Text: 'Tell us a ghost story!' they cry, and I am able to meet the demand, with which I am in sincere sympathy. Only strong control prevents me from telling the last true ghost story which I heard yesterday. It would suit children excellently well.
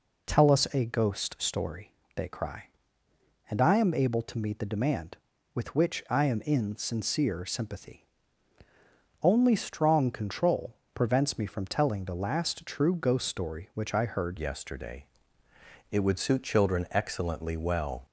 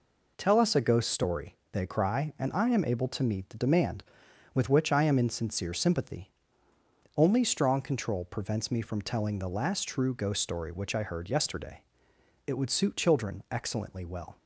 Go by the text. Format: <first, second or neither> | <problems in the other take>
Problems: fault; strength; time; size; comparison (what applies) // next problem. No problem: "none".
second | pauses between "control" and "prevents"; slight; at 10.7 s; 0.18 s long // changes voice at "yesterday"; from 14.3 s on; 3.7 s long